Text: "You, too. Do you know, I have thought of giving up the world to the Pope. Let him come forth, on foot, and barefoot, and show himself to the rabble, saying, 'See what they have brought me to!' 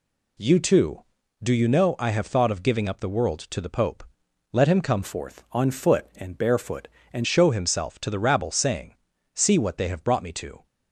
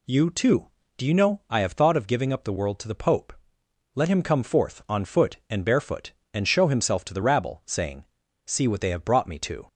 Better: second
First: changes voice from "forth" to "and"; from 5.0 to 7.2 s; 2.2 s long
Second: none

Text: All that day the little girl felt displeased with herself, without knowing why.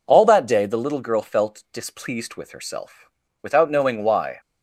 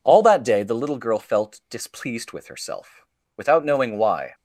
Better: neither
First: none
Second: none

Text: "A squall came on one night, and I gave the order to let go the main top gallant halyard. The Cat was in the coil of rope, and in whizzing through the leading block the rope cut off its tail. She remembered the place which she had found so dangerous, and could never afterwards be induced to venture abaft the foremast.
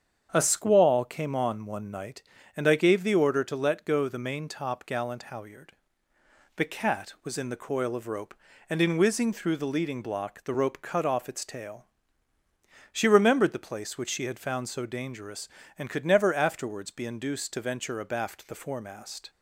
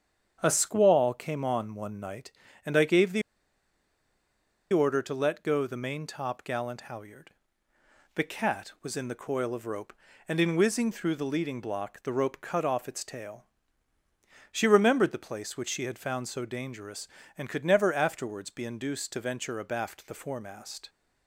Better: first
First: starts louder than the rest; strong; until 1.3 s; 8 dB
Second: starts louder than the rest; strong; until 1.4 s; 8 dB // pauses between "the" and "order"; strong; at 3.2 s; 1.5 s long

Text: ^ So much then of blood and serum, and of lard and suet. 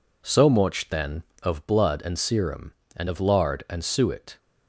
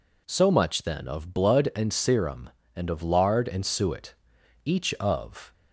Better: first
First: none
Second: goes on to say "Each of"; noticeable; from 4.6 s on; 0.88 s long

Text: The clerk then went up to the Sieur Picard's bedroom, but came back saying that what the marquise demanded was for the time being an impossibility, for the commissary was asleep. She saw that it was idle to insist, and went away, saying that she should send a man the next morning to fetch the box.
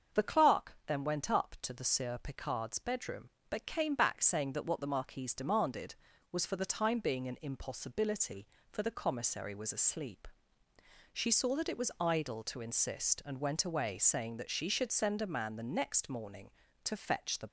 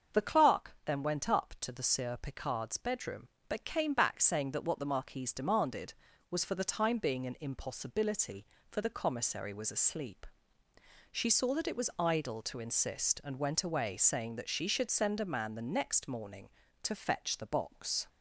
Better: second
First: starts louder than the rest; until 1.2 s; 6.5 dB // stops before "box"; at 17.4 s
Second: starts louder than the rest; until 1.2 s; 7 dB

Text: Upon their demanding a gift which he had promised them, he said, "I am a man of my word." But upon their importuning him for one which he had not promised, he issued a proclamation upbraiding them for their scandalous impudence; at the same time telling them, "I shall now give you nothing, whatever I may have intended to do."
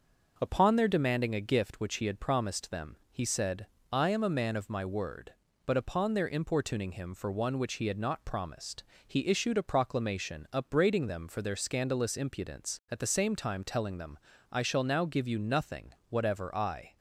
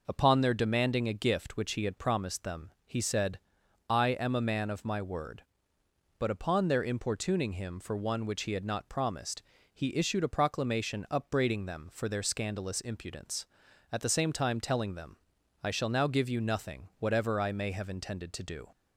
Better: second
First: starts louder than the rest; noticeable; until 1.3 s; 6 dB // stops before "may have intended to do"; at 16.9 s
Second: none

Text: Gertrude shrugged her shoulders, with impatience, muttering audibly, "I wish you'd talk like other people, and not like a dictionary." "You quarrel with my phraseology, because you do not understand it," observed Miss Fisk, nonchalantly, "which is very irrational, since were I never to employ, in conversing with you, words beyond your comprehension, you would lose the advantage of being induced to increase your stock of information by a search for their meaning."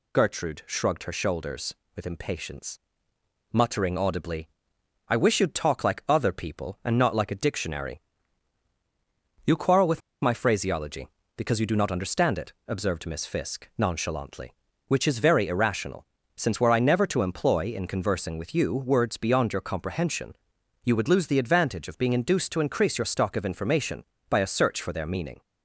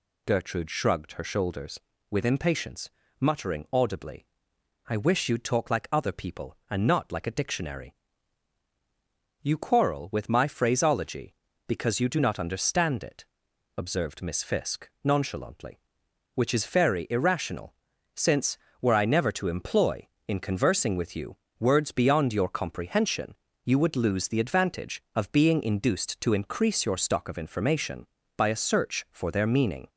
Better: second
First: pauses between "with" and "my"; slight; at 10.0 s; 0.22 s long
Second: none

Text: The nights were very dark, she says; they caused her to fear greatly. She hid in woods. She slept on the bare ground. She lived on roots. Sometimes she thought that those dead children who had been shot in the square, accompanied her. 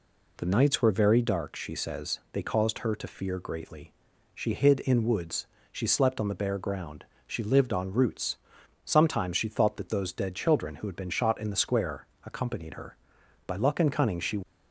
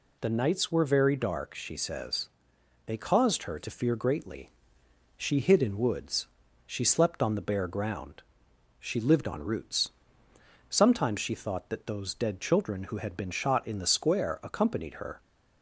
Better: second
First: goes on to say "By luck and cunning she"; noticeable; from 13.4 s on; 0.96 s long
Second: none

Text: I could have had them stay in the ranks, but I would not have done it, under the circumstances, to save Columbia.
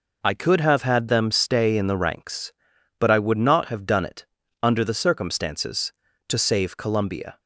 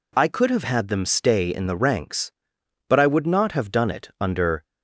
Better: first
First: none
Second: stops before "the circumstances to save Columbia"; at 4.6 s

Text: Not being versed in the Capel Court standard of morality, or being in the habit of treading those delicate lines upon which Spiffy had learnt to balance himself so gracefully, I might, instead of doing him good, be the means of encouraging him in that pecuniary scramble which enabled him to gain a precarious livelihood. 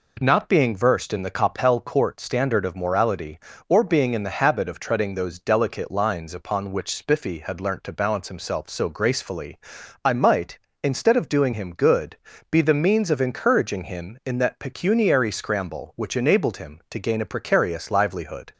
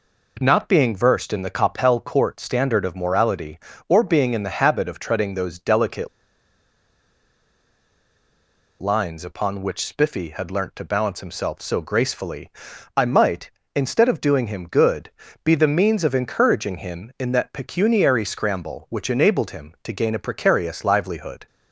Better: first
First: none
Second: pauses between "delicate" and "lines"; strong; at 6.0 s; 2.7 s long

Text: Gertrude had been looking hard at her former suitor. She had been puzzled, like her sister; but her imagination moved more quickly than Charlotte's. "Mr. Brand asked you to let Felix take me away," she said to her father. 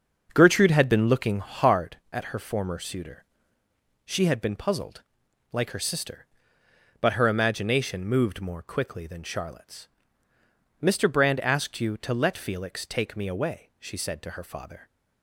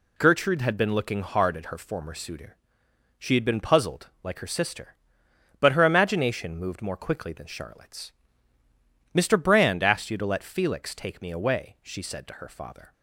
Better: second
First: starts louder than the rest; until 1.7 s; 6.5 dB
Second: none

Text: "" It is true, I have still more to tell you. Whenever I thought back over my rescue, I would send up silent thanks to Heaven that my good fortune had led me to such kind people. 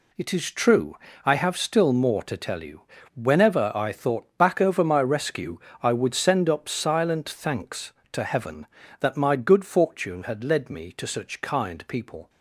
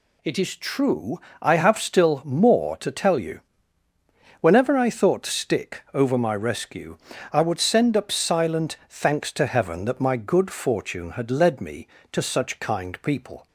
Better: first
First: none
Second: says "stick" for "back"; at 5.2 s

